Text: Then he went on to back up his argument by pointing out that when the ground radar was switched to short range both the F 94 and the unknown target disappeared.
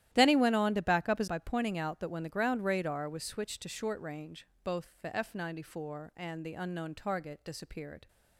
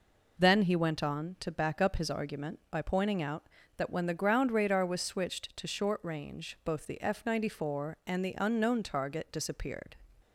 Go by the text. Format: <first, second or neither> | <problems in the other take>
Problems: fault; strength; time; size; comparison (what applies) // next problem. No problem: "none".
second | starts louder than the rest; strong; until 1.1 s; 12.5 dB // skips "argument"; at 1.2 s // pauses between "range" and "both"; slight; at 4.4 s; 0.18 s long